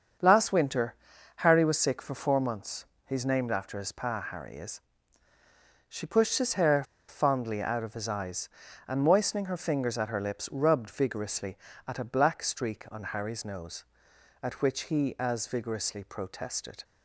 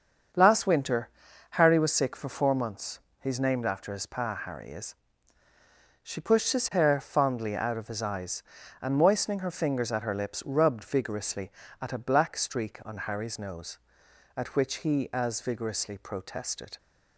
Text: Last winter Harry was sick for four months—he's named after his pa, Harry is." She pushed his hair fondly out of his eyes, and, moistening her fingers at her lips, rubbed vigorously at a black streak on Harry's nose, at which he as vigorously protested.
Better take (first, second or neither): second